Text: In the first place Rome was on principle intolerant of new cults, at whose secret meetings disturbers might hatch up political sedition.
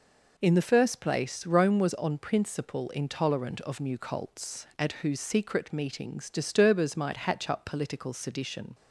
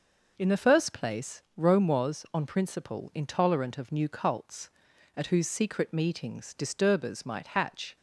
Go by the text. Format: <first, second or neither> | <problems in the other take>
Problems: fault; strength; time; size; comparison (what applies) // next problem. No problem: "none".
first | stops before "up political sedition"; at 7.9 s